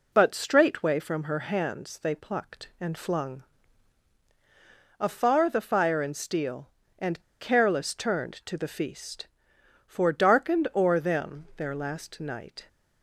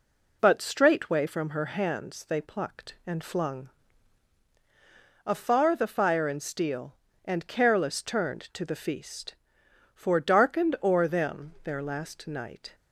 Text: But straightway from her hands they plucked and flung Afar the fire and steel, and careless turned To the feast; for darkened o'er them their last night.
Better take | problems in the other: second | pauses between "flung" and "Afar"; strong; at 3.4 s; 1.5 s long; strong in the second // pauses between "and" and "careless"; slight; at 7.1 s; 0.21 s long

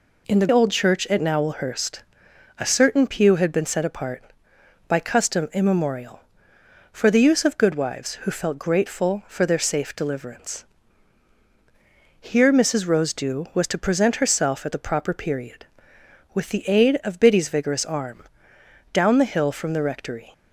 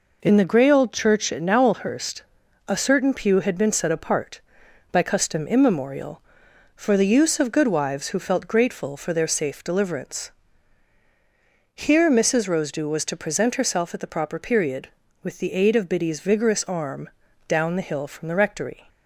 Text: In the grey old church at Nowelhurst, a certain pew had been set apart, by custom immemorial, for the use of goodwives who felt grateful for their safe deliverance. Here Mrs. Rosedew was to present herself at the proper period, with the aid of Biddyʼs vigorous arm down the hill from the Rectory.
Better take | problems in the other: second | skips "grey"; at 0.4 s // pauses between "arm" and "down"; noticeable; at 18.2 s; 0.70 s long; also in the second

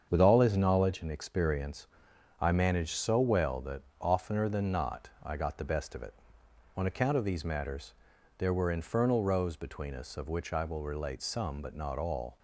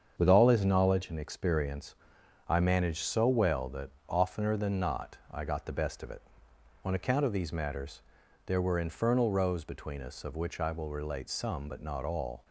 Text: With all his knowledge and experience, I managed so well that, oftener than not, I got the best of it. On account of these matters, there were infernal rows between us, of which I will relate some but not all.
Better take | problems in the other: neither | starts louder than the rest; strong; the same in both

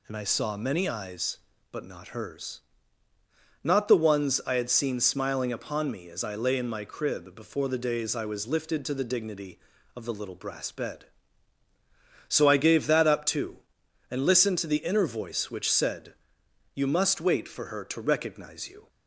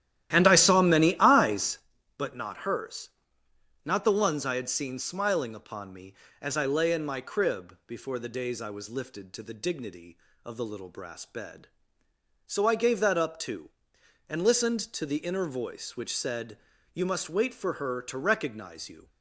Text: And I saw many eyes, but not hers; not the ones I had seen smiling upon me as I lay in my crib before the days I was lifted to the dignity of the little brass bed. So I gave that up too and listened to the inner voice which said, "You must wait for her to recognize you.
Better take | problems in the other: first | starts louder than the rest; strong; until 1.8 s; 12.5 dB

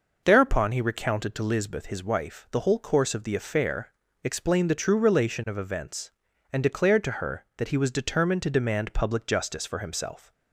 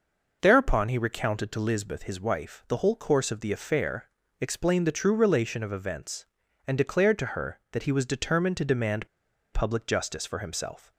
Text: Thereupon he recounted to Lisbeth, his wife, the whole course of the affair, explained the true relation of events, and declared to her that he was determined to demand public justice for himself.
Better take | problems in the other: first | pauses between "demand" and "public"; at 9.0 s; 0.45 s long

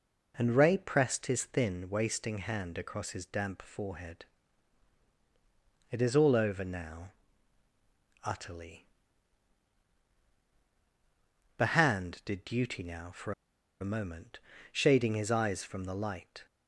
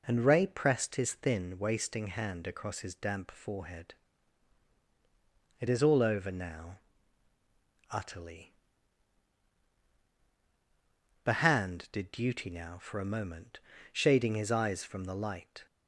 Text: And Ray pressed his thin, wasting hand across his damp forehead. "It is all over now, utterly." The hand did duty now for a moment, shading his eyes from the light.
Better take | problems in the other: second | pauses between "for" and "a"; noticeable; at 13.3 s; 0.49 s long

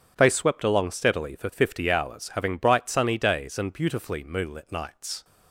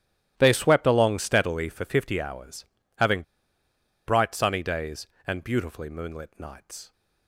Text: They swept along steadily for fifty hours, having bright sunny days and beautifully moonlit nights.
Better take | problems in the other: first | starts louder than the rest; strong; until 1.3 s; 13 dB; strong in the first // pauses between "having" and "bright"; noticeable; at 3.2 s; 0.84 s long

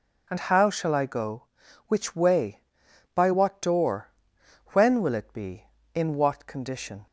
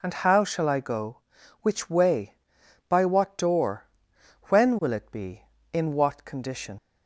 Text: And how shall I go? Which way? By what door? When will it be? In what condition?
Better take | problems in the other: first | leaves "condition" unfinished; at 6.7 s; 55 ms

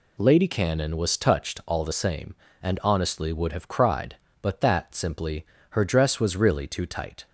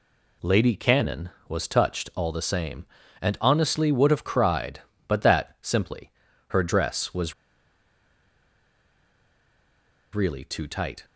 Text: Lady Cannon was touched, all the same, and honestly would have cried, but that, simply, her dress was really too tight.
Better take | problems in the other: first | pauses between "was" and "really"; strong; at 7.3 s; 2.8 s long

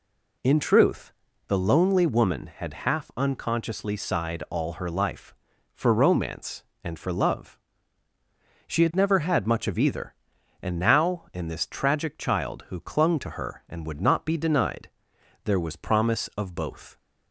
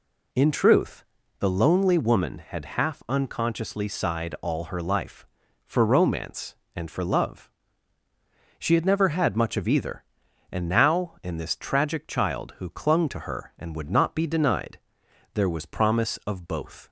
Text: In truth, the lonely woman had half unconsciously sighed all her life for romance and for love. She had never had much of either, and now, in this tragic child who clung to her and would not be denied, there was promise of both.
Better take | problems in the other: neither | none

